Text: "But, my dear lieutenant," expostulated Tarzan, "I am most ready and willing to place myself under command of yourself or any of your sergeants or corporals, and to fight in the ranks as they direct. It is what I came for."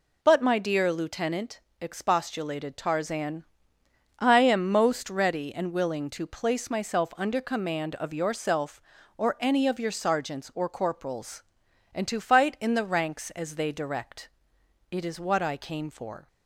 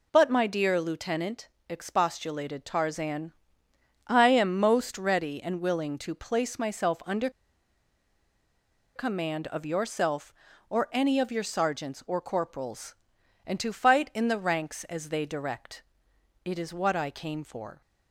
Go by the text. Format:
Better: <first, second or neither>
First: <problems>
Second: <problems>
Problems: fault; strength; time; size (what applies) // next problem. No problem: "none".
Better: first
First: none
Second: pauses between "under" and "command"; strong; at 7.2 s; 1.6 s long